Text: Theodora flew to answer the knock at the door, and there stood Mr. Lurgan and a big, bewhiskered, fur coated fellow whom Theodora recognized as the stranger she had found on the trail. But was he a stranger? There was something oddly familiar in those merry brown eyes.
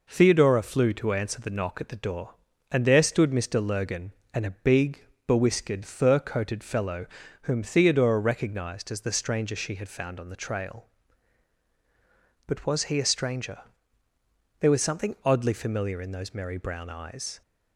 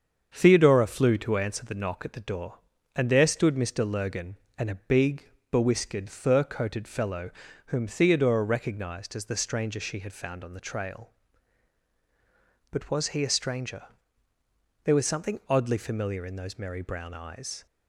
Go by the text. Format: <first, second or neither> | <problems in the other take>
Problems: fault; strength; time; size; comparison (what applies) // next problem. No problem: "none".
first | starts louder than the rest; strong; until 1.5 s; 7 dB // pauses between "fellow" and "whom"; slight; at 7.2 s; 0.36 s long; slight in the first